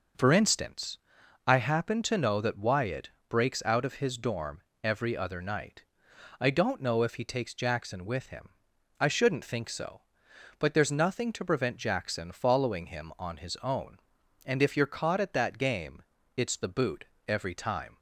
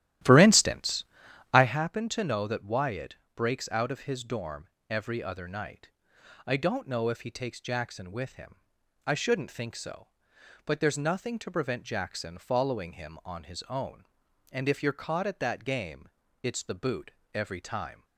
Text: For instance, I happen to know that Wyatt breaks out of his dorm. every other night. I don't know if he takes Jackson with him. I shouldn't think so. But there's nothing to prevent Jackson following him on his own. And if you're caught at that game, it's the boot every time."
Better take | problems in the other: first | starts louder than the rest; strong; until 1.8 s; 13 dB // pauses between "Wyatt" and "breaks"; slight; at 3.1 s; 0.18 s long; slight in the first // pauses between "boot" and "every"; slight; at 17.1 s; 0.22 s long; slight in the first

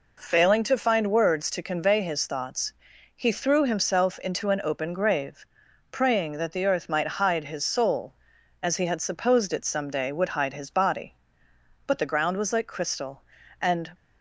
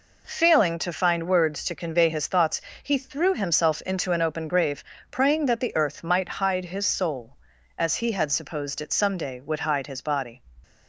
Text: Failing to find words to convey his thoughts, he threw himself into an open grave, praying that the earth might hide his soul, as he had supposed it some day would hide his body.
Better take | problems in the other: second | goes on to say "But the ground was like crystal and"; strong; from 11.8 s on; 2.0 s long

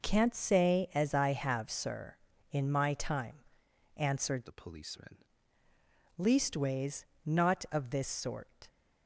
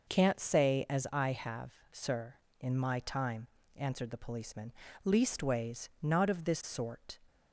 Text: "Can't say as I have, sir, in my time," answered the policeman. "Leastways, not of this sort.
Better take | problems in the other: second | changes voice from "the" to "policeman"; from 4.4 to 5.2 s; 0.8 s long

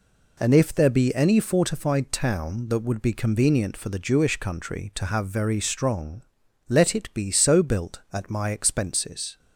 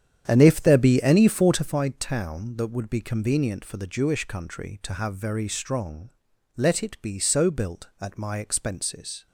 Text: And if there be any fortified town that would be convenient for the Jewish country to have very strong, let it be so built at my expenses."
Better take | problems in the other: first | starts louder than the rest; strong; until 1.9 s; 9 dB

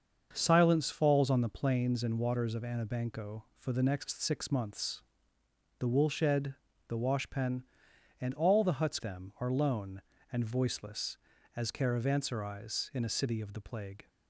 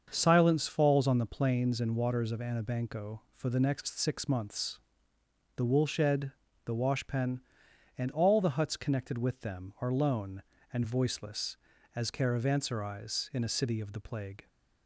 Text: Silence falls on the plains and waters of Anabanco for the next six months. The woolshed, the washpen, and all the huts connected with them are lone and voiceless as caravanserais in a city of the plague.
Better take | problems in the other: second | starts louder than the rest; until 1.3 s; 6.5 dB; also in the second // skips "connected with"; at 8.9 s

